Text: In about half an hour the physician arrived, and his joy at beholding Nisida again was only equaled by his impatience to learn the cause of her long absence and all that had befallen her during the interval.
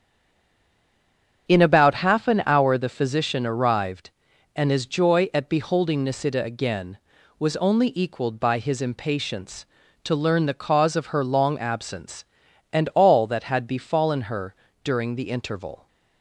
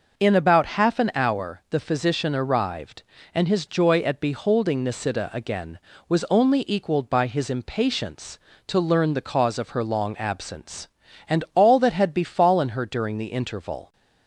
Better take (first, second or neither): second